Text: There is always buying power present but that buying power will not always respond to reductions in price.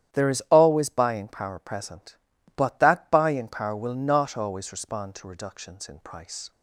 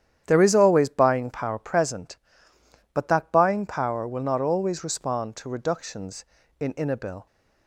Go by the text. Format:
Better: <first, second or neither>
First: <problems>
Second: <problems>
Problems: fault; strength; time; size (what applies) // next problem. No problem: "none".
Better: first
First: starts louder than the rest; strong; until 1.2 s; 10.5 dB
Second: starts louder than the rest; strong; until 1.2 s; 10 dB // says "inabil" for "price"; at 6.7 s